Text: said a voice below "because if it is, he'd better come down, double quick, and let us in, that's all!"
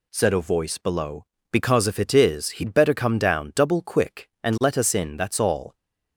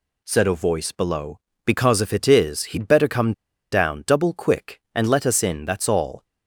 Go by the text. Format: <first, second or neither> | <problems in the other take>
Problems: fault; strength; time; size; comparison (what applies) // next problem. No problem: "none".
first | pauses between "come" and "down"; at 3.3 s; 0.39 s long